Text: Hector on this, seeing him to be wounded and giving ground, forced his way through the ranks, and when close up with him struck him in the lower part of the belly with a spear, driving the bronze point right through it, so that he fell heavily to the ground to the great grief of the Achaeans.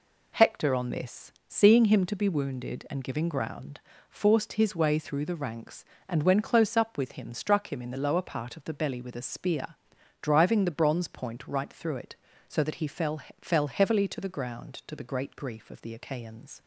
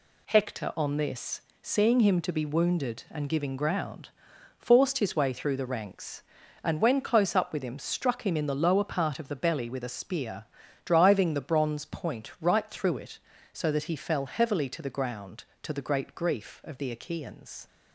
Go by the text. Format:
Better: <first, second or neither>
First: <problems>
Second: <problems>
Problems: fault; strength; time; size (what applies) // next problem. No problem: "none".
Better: second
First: says "fell" twice; at 13.3 s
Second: none